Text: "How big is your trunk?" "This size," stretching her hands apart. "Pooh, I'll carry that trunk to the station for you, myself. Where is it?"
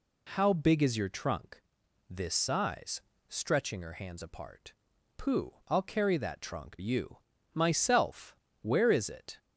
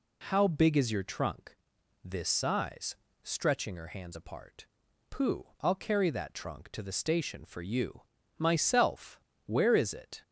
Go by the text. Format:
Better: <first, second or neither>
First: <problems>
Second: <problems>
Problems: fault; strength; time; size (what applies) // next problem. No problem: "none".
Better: second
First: skips "to the station for"; at 6.7 s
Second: none